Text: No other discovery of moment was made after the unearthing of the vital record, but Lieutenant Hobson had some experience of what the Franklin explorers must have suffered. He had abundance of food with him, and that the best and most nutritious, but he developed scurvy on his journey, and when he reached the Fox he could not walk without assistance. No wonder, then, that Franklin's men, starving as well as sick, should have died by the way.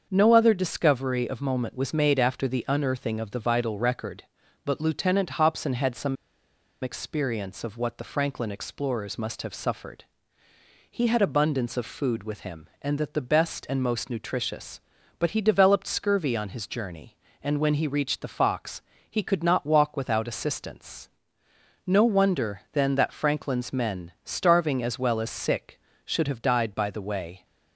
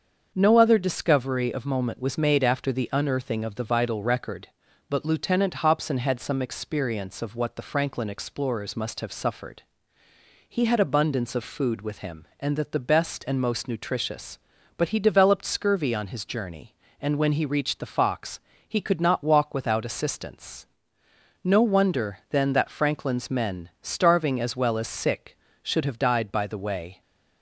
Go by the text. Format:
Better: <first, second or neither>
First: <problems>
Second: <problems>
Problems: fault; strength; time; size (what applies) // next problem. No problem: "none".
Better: second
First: starts louder than the rest; until 1.1 s; 7 dB // pauses between "some" and "experience"; noticeable; at 6.1 s; 0.66 s long // pauses between "Fox" and "he"; slight; at 18.8 s; 0.28 s long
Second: starts louder than the rest; until 1.3 s; 6.5 dB // pauses between "Fox" and "he"; slight; at 18.3 s; 0.28 s long